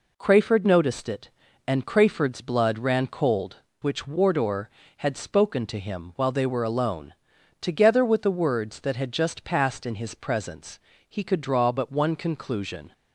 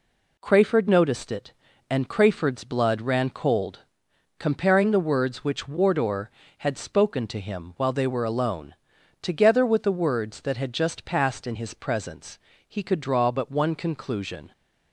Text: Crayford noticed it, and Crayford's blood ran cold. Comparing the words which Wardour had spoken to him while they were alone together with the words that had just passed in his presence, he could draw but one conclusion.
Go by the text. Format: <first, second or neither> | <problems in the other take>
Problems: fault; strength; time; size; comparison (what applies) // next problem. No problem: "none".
second | skips "Comparing the words"; at 3.6 s // pauses between "alone" and "together"; at 7.1 s; 0.44 s long; also in the second